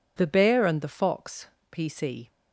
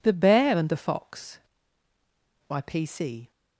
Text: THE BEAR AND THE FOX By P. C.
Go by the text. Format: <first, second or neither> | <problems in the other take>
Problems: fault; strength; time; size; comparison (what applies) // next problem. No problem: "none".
second | skips "By"; at 1.5 s